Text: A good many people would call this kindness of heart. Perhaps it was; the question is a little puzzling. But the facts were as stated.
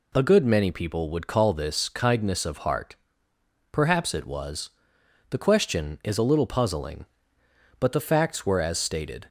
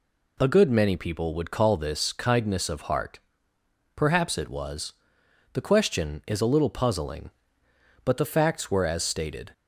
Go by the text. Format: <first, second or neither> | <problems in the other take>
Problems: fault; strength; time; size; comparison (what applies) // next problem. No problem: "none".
neither | none